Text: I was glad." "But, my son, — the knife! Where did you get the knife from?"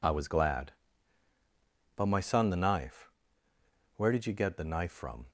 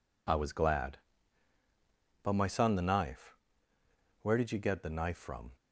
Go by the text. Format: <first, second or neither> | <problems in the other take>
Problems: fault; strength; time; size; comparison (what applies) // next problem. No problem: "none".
neither | none